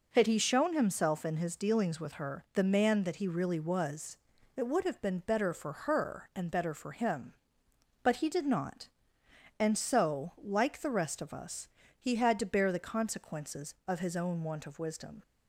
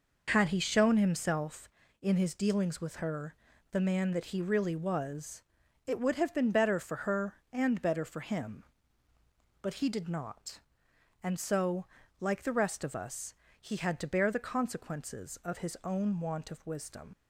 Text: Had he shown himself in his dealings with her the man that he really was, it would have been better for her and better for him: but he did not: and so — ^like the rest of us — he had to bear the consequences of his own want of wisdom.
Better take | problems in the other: first | pauses between "her" and "the"; at 3.3 s; 0.38 s long // leaves "wisdom" unfinished; at 17.1 s; 80 ms

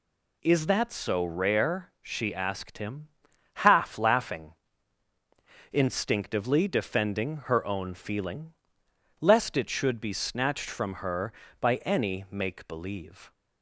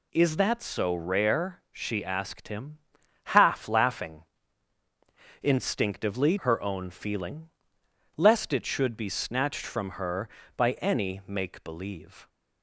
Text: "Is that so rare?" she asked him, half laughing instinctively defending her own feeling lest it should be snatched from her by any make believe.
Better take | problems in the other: first | pauses between "laughing" and "instinctively"; at 4.2 s; 1.1 s long; also in the first // skips "defending"; at 6.3 s // pauses between "feeling" and "lest"; noticeable; at 7.4 s; 0.66 s long; noticeable in the first

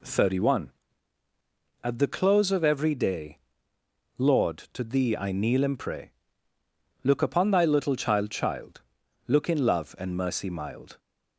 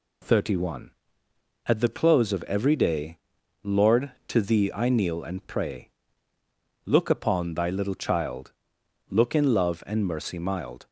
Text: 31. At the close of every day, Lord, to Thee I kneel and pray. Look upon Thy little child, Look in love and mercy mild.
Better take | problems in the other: second | says "child" twice; at 8.3 s

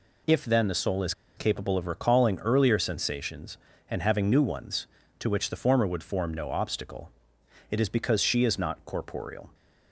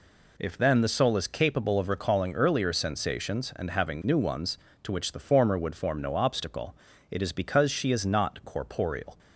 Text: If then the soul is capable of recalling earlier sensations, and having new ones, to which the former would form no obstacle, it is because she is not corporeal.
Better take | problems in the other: second | pauses between "is" and "capable"; slight; at 1.1 s; 0.22 s long

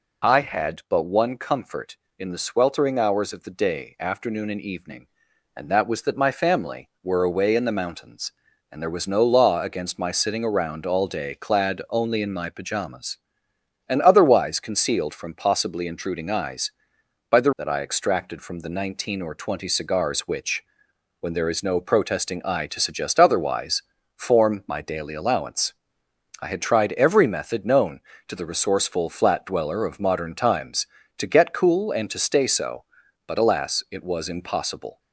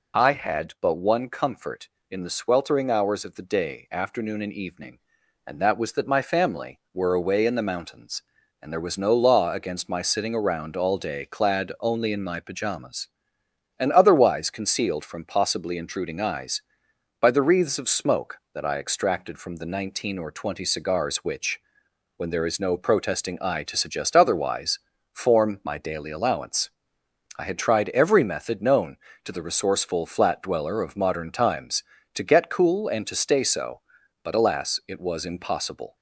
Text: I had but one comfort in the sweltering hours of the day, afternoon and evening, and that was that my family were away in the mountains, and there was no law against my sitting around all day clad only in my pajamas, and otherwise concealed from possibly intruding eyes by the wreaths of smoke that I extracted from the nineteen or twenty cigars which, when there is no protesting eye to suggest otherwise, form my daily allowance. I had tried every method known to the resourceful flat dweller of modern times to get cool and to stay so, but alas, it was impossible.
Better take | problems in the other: second | skips "wreaths of smoke"; at 17.5 s

